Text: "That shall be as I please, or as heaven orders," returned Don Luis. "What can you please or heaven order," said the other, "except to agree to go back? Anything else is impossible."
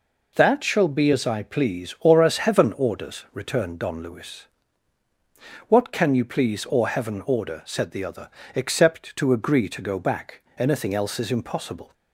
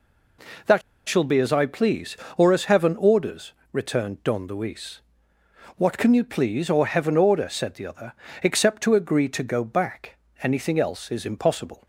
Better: first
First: none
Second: pauses between "That" and "shall"; slight; at 0.8 s; 0.27 s long

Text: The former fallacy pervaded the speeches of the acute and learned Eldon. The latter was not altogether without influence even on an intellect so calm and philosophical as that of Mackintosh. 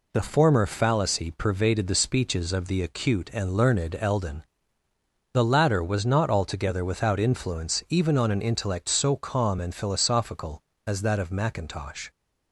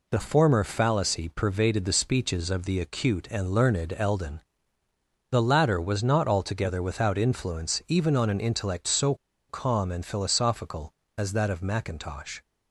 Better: first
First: none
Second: pauses between "so" and "calm"; slight; at 9.1 s; 0.33 s long

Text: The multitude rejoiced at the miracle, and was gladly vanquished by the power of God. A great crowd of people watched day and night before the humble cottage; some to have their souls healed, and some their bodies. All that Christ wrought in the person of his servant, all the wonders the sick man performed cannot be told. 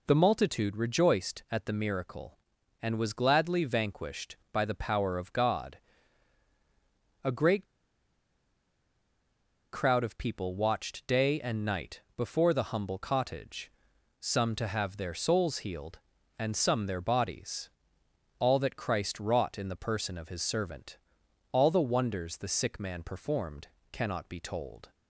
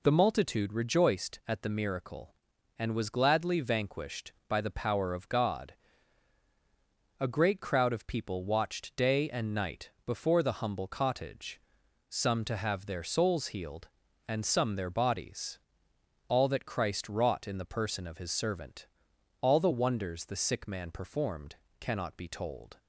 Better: second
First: pauses between "great" and "crowd"; strong; at 7.6 s; 2.0 s long // pauses between "night" and "before"; slight; at 12.0 s; 0.16 s long // pauses between "performed" and "cannot"; slight; at 23.6 s; 0.22 s long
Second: pauses between "night" and "before"; slight; at 9.9 s; 0.16 s long // pauses between "performed" and "cannot"; slight; at 21.5 s; 0.22 s long

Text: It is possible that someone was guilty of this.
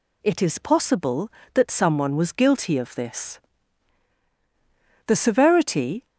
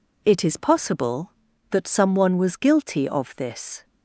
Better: second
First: goes on to say "The severity"; noticeable; from 5.0 s on; 0.98 s long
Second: none

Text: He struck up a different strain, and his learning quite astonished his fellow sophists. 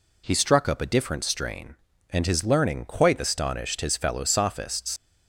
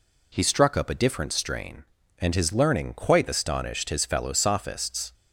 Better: second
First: leaves "sophists" unfinished; at 4.9 s; 80 ms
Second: none

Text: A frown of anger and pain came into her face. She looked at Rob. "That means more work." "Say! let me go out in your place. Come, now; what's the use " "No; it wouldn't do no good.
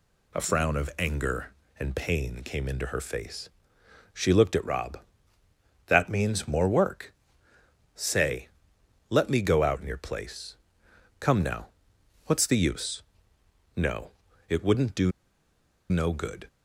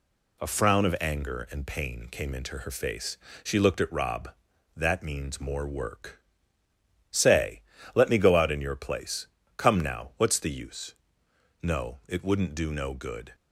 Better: second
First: pauses between "do" and "no"; noticeable; at 15.1 s; 0.79 s long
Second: none

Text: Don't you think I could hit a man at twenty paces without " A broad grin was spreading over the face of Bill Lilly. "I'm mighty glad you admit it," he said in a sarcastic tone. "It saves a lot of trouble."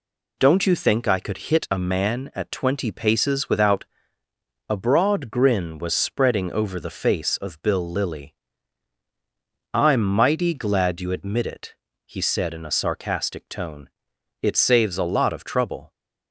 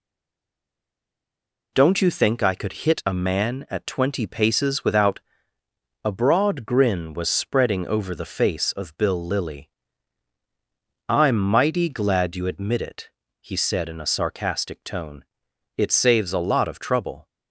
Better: first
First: none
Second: stays silent before the first word; noticeable; until 1.7 s; 1.7 s long

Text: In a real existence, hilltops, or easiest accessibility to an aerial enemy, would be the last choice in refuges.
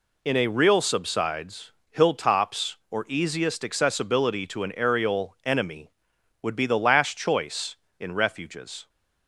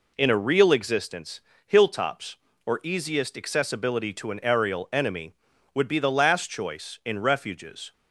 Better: second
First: says "subsides" for "existence"; at 0.8 s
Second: none

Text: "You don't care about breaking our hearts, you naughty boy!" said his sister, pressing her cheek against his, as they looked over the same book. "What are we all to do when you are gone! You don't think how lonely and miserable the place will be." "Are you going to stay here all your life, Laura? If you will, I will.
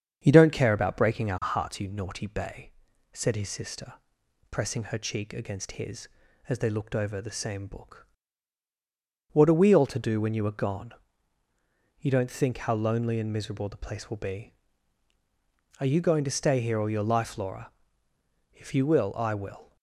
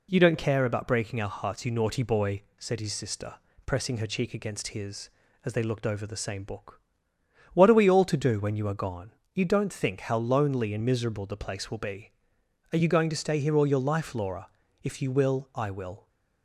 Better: second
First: starts louder than the rest; strong; until 1.2 s; 7.5 dB // says "bay" for "boy"; at 2.2 s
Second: none

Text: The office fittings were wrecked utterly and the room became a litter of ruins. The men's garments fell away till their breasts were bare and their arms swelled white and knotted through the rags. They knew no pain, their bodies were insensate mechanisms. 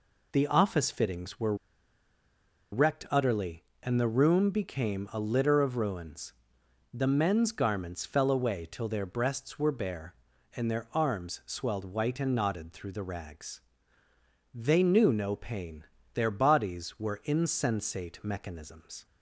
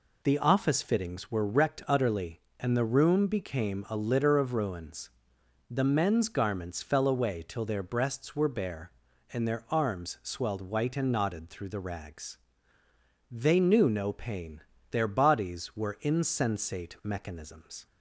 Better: second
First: pauses between "were" and "wrecked"; at 1.5 s; 1.1 s long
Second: none

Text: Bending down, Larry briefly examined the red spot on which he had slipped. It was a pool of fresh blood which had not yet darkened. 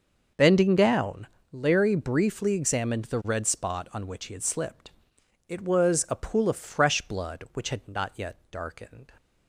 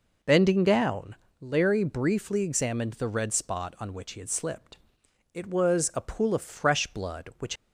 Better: first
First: none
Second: stops before "had not yet darkened"; at 7.5 s

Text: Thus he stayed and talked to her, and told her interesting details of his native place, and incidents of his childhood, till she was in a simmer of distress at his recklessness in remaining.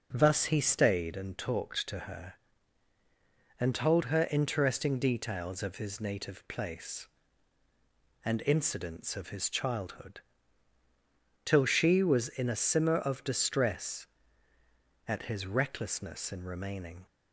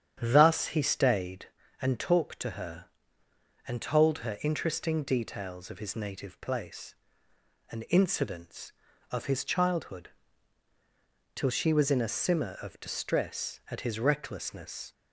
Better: first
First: none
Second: starts louder than the rest; strong; until 1.2 s; 8.5 dB // stops before "in remaining"; at 14.9 s

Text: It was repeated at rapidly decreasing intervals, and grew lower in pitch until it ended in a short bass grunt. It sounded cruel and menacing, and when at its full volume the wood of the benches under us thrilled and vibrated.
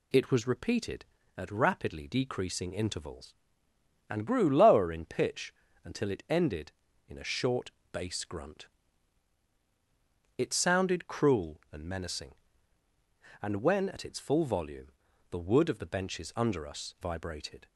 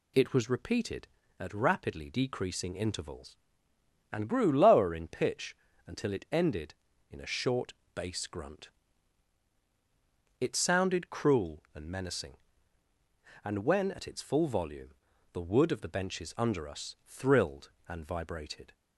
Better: second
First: pauses between "pitch" and "until"; slight; at 5.5 s; 0.30 s long // pauses between "short" and "bass"; slight; at 7.7 s; 0.22 s long // pauses between "volume" and "the"; at 14.8 s; 0.42 s long // skips "thrilled and"; at 16.9 s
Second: pauses between "pitch" and "until"; slight; at 5.5 s; 0.30 s long // pauses between "short" and "bass"; slight; at 7.7 s; 0.22 s long // pauses between "volume" and "the"; at 14.9 s; 0.42 s long

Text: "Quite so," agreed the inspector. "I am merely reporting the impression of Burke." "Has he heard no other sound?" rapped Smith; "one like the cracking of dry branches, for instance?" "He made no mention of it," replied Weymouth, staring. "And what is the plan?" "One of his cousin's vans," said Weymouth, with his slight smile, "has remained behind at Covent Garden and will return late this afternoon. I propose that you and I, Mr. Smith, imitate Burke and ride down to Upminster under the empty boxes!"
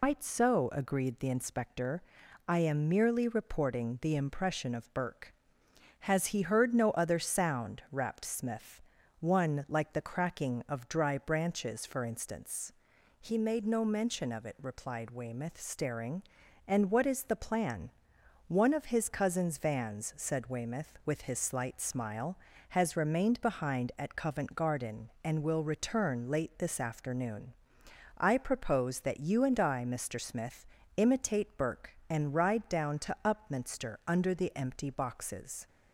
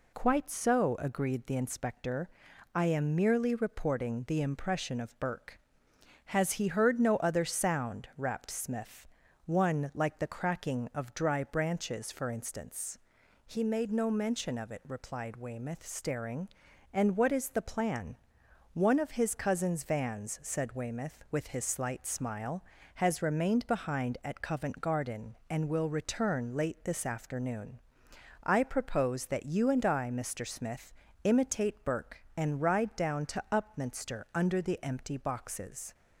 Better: second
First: loses the start of "Quite"; at 0.0 s; 150 ms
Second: none

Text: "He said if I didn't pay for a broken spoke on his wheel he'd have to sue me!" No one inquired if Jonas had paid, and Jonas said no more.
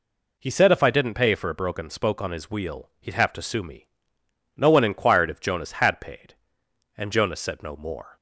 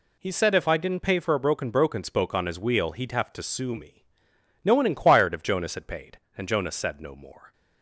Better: first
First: none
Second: says "broken" twice; at 1.6 s

